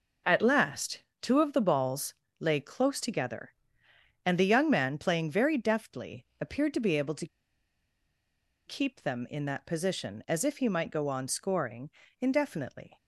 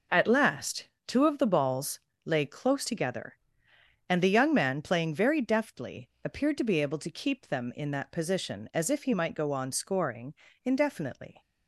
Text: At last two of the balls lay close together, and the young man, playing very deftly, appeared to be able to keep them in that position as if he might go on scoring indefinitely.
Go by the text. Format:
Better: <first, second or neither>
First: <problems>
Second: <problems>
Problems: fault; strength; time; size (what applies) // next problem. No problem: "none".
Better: second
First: pauses between "last" and "two"; slight; at 1.0 s; 0.18 s long // pauses between "balls" and "lay"; slight; at 2.1 s; 0.24 s long // pauses between "to" and "keep"; strong; at 7.2 s; 1.4 s long // pauses between "scoring" and "indefinitely"; slight; at 11.8 s; 0.32 s long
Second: pauses between "last" and "two"; slight; at 0.8 s; 0.18 s long // pauses between "balls" and "lay"; slight; at 1.9 s; 0.24 s long // pauses between "scoring" and "indefinitely"; slight; at 10.3 s; 0.32 s long